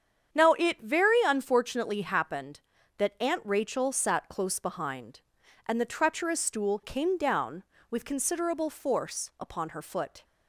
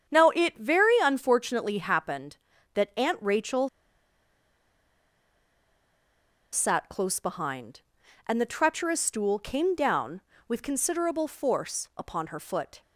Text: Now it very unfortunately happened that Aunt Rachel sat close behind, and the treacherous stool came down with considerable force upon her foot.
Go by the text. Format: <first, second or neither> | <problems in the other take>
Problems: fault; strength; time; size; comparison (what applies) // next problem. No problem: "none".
first | starts louder than the rest; strong; until 1.2 s; 8 dB; strong in the first // pauses between "Rachel" and "sat"; strong; at 3.6 s; 2.8 s long